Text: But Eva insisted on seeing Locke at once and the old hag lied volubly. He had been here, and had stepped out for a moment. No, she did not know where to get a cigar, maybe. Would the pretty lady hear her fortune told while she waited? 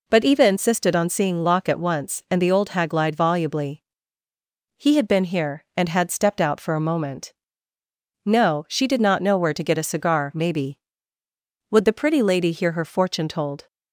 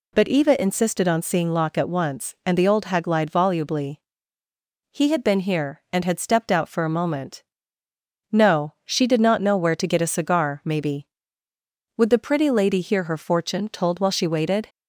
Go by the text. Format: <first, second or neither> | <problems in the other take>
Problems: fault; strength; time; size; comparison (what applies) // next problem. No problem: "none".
second | stops before "while she waited"; at 13.6 s